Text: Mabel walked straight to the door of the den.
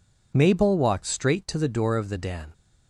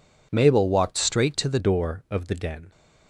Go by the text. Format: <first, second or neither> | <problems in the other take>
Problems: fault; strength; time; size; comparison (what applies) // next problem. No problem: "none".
first | changes voice at "door"; from 1.5 s on; 1.2 s long